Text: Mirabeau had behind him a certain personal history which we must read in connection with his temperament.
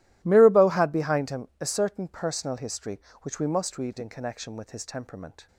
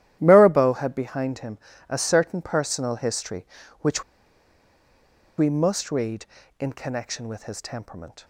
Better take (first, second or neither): first